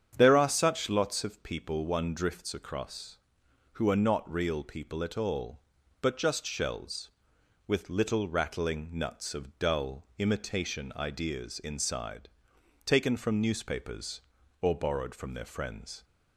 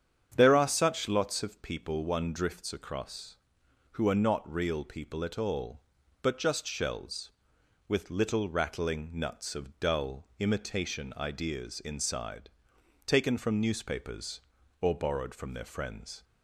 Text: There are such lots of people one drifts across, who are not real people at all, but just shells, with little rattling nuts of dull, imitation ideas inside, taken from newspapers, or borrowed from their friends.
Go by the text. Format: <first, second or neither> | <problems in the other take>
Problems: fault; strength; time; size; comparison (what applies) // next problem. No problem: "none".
neither | starts louder than the rest; strong; the same in both